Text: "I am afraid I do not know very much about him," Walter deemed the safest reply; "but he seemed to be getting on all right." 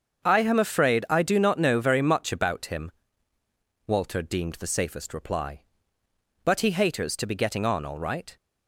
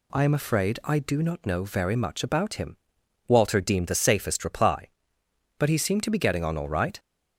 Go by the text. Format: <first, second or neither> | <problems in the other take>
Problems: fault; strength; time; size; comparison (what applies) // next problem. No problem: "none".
second | starts louder than the rest; until 1.2 s; 6.5 dB // says "haters" for "seemed"; at 6.7 s